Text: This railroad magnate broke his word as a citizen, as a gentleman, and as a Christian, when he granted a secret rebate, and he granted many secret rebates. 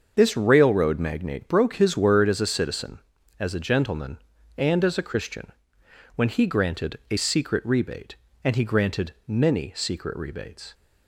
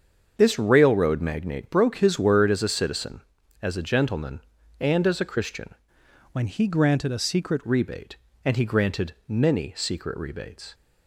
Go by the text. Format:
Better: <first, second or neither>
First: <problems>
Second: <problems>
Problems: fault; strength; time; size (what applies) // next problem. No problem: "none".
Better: first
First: starts louder than the rest; until 1.1 s; 6.5 dB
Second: starts louder than the rest; until 1.3 s; 7 dB // changes voice from "when" to "secret"; from 6.3 to 7.5 s; 1.2 s long